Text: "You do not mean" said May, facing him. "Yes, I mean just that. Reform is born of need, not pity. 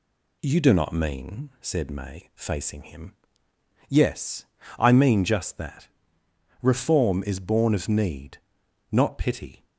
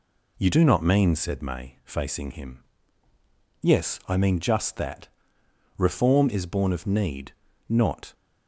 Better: first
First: none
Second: stops before "pity"; at 8.1 s

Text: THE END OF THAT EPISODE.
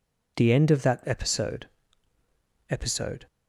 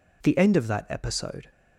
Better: second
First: says "EPISODE" twice; at 2.6 s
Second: none

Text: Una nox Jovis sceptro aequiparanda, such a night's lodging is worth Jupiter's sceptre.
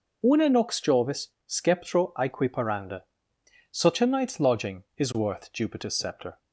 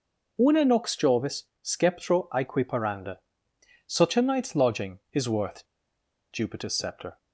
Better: first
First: pauses between "Jovis" and "sceptro"; slight; at 1.2 s; 0.18 s long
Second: pauses between "Jovis" and "sceptro"; slight; at 1.4 s; 0.18 s long // pauses between "worth" and "Jupiter's"; noticeable; at 5.6 s; 0.66 s long

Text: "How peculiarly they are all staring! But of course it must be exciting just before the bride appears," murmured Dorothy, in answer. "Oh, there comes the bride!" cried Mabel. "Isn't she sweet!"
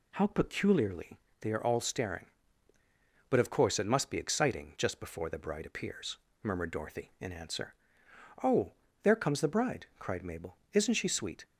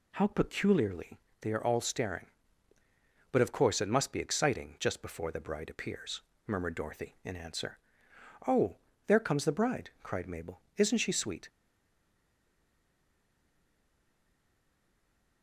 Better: first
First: pauses between "peculiarly" and "they"; slight; at 1.1 s; 0.22 s long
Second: pauses between "peculiarly" and "they"; slight; at 1.1 s; 0.22 s long // stays silent after the last word; strong; from 11.4 s on; 4.0 s long

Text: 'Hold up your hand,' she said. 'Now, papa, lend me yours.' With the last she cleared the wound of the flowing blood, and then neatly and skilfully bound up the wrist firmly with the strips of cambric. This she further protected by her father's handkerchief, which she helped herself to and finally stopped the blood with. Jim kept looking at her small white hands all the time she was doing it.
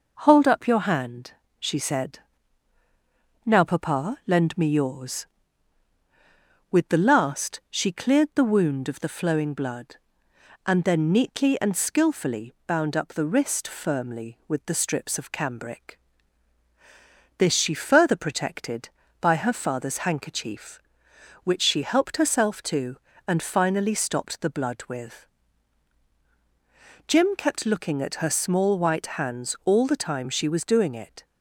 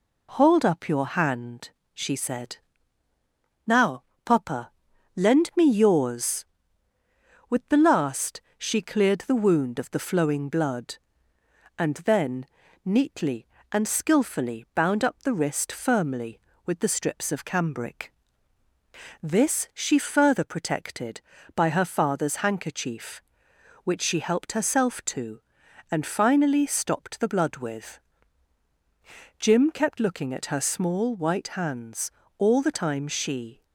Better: first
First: none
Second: pauses between "last" and "she"; slight; at 8.3 s; 0.16 s long // pauses between "then" and "neatly"; at 12.4 s; 0.40 s long // pauses between "hands" and "all"; slight; at 32.0 s; 0.28 s long // stops before "was doing it"; at 33.6 s

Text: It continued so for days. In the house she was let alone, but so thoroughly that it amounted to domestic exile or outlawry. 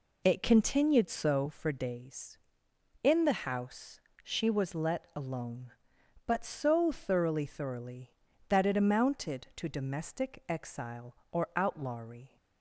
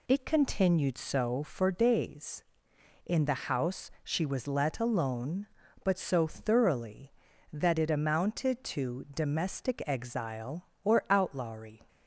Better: second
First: pauses between "house" and "she"; slight; at 3.9 s; 0.24 s long // says "thoroughly" twice; at 7.4 s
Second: none

